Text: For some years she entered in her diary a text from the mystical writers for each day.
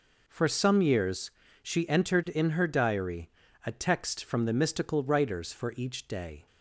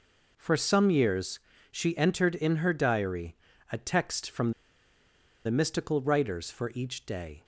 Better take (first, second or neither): first